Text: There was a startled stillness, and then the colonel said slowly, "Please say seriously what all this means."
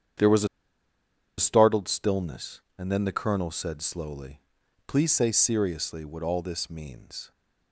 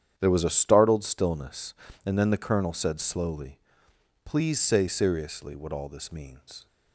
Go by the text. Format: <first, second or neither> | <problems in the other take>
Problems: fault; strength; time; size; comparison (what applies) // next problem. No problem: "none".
second | starts louder than the rest; strong; until 2.1 s; 8.5 dB; strong in the second // pauses between "a" and "startled"; noticeable; at 0.4 s; 0.91 s long